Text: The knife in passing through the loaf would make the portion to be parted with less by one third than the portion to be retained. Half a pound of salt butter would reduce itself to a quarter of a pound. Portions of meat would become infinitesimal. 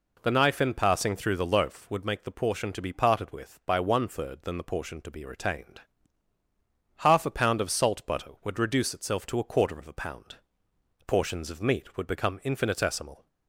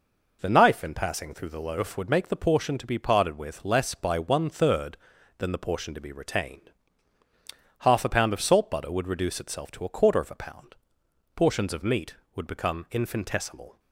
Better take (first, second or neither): second